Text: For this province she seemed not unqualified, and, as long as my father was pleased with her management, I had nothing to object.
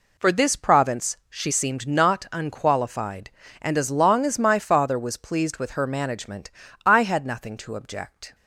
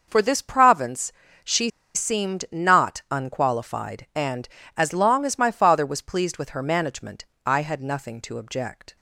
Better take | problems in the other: first | pauses between "province" and "she"; slight; at 1.1 s; 0.34 s long // pauses between "she" and "seemed"; slight; at 1.6 s; 0.25 s long

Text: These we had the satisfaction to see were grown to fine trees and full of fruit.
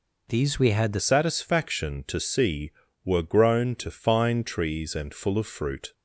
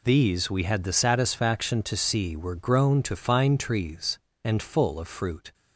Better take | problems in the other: second | changes voice at "satisfaction"; from 0.9 s on; 5.0 s long

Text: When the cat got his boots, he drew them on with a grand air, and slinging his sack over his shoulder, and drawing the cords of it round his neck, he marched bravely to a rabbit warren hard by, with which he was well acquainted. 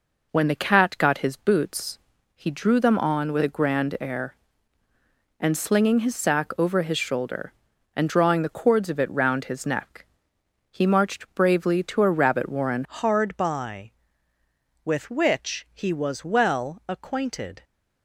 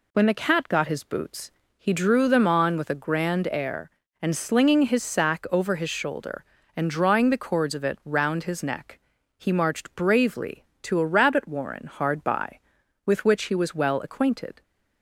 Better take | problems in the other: second | changes voice at "hard"; from 12.8 s on; 4.8 s long

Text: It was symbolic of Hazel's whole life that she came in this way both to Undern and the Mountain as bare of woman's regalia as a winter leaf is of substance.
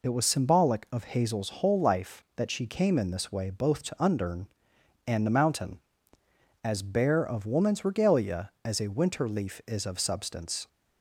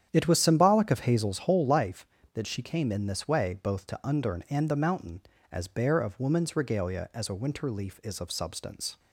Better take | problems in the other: first | starts louder than the rest; strong; until 1.9 s; 9.5 dB

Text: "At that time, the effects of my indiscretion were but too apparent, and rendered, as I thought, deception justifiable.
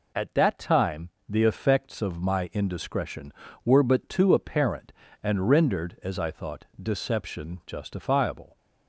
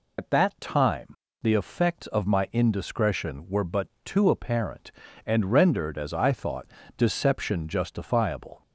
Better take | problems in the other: first | loses the start of "At"; at 0.1 s; 105 ms // pauses between "but" and "too"; slight; at 3.8 s; 0.16 s long

